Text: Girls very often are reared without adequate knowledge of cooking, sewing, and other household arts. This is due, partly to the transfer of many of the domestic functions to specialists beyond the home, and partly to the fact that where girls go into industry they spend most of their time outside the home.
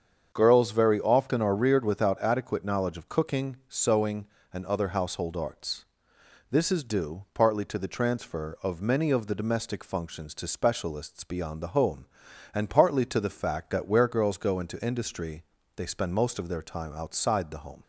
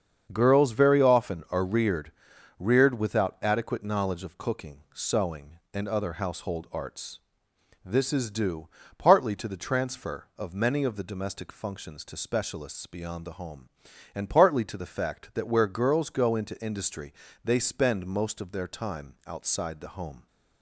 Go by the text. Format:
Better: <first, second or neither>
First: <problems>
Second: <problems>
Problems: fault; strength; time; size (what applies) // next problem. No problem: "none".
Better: first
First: starts louder than the rest; strong; until 1.3 s; 7.5 dB // pauses between "industry" and "they"; slight; at 15.4 s; 0.34 s long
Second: starts louder than the rest; until 1.3 s; 7 dB // says "reared" twice; at 2.5 s // pauses between "industry" and "they"; slight; at 17.1 s; 0.32 s long